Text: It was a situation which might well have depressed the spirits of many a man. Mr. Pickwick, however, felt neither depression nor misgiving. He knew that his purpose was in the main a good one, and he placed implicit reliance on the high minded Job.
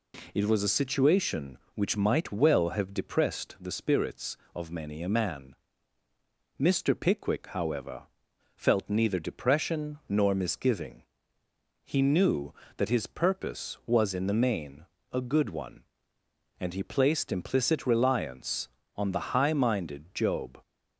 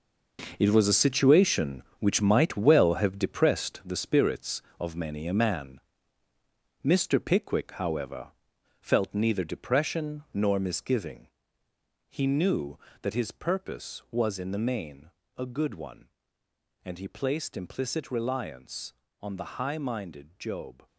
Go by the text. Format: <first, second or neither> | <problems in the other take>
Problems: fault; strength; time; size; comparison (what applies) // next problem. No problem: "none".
first | gets quieter; strong; throughout; 11 dB // pauses between "main" and "a"; slight; at 15.0 s; 0.26 s long; slight in the first